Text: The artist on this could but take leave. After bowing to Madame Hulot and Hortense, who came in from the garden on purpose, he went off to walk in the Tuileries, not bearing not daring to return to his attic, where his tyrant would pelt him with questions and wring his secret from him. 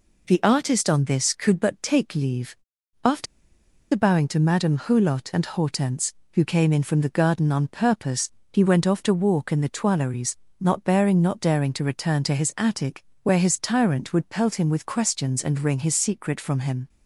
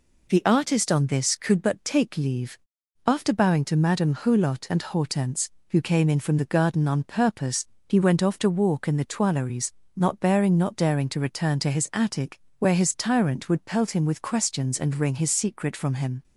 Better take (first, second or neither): second